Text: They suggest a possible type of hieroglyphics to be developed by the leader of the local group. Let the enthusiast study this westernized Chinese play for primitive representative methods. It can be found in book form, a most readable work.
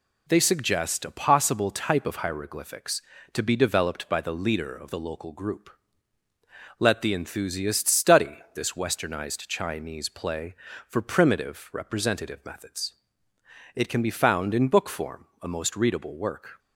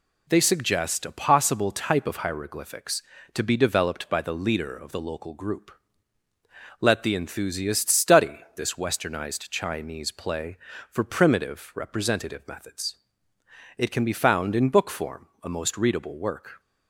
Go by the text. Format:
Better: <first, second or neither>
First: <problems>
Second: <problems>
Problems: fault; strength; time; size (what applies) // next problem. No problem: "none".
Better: neither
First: pauses between "study" and "this"; slight; at 8.3 s; 0.16 s long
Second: pauses between "study" and "this"; slight; at 8.3 s; 0.16 s long